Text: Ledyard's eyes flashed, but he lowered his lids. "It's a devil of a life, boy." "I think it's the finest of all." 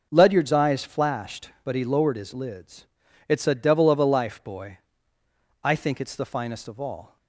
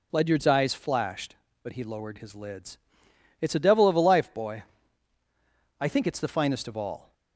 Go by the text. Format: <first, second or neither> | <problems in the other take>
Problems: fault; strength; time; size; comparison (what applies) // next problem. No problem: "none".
neither | none